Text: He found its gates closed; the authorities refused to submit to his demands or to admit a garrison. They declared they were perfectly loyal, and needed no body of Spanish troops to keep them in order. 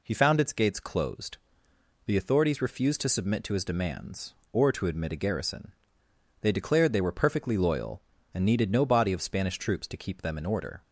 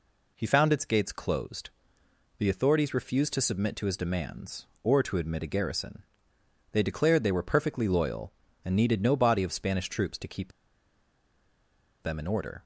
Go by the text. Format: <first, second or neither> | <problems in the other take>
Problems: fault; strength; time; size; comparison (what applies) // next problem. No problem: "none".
first | pauses between "keep" and "them"; strong; at 10.5 s; 1.5 s long